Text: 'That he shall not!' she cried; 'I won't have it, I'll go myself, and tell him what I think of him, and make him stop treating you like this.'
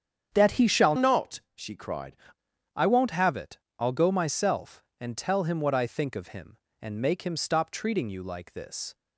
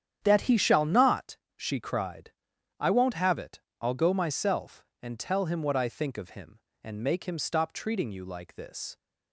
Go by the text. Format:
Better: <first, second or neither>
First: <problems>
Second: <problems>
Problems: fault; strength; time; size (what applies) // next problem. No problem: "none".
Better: second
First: starts louder than the rest; strong; until 1.3 s; 8.5 dB // changes voice from "not" to "cried"; from 0.9 to 2.1 s; 1.2 s long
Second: starts louder than the rest; strong; until 1.2 s; 9.5 dB